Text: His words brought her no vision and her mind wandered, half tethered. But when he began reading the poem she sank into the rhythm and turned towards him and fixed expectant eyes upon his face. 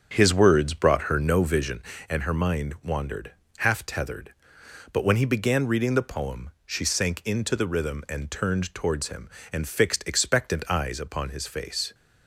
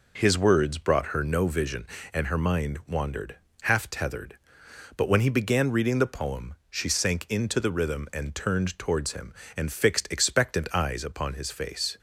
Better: second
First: starts louder than the rest; strong; until 1.8 s; 7 dB // pauses between "poem" and "she"; slight; at 6.4 s; 0.16 s long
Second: pauses between "poem" and "she"; slight; at 6.5 s; 0.16 s long

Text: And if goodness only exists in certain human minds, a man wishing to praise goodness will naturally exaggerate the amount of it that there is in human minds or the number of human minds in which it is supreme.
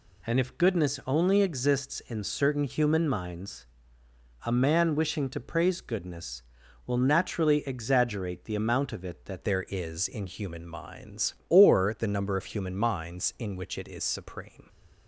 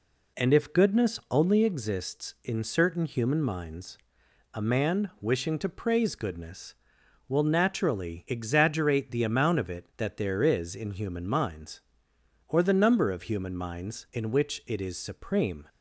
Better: second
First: changes voice at "there"; from 9.4 s on; 5.2 s long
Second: none

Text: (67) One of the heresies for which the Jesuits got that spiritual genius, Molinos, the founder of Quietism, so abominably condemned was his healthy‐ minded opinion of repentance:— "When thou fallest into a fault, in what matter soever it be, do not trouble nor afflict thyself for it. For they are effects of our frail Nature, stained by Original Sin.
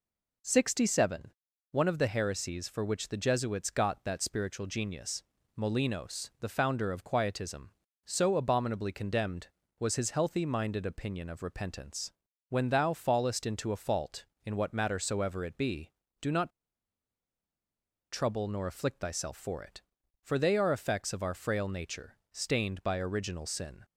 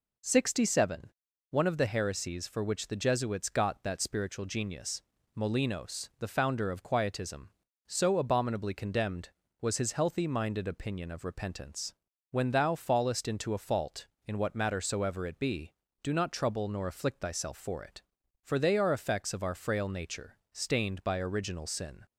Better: second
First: pauses between "not" and "trouble"; strong; at 16.4 s; 1.6 s long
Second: none

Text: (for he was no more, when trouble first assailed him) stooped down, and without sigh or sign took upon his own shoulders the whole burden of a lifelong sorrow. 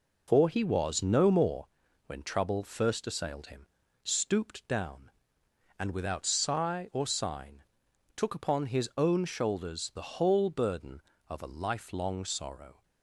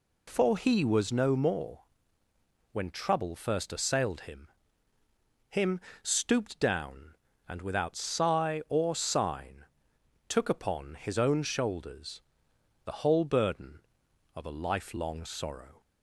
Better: first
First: pauses between "sign" and "took"; noticeable; at 7.6 s; 0.52 s long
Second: says "him" twice; at 5.5 s // pauses between "sign" and "took"; noticeable; at 9.6 s; 0.64 s long // pauses between "shoulders" and "the"; noticeable; at 12.2 s; 0.64 s long

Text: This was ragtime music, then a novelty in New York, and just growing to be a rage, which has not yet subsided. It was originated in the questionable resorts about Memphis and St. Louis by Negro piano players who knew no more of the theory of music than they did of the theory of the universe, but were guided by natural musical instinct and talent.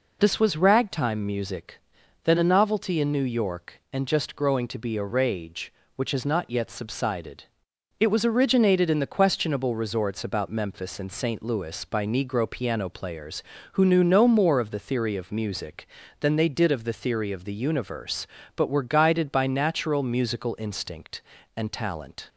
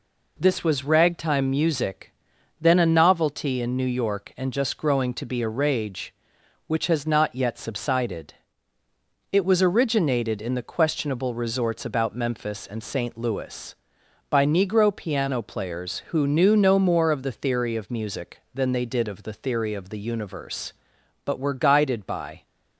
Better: first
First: none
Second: stops before "natural musical instinct and talent"; at 22.4 s

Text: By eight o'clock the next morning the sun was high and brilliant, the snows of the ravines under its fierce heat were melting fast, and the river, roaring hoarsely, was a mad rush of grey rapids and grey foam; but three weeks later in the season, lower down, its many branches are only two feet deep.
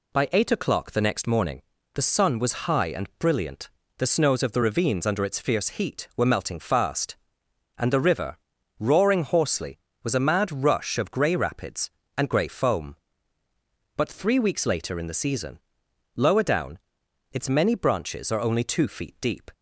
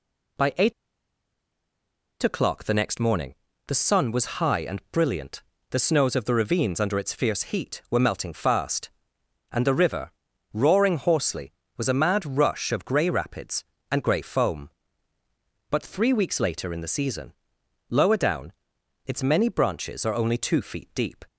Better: first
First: pauses between "morning" and "the"; slight; at 1.6 s; 0.34 s long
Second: pauses between "eight" and "o'clock"; strong; at 0.7 s; 1.5 s long // pauses between "morning" and "the"; slight; at 3.3 s; 0.34 s long

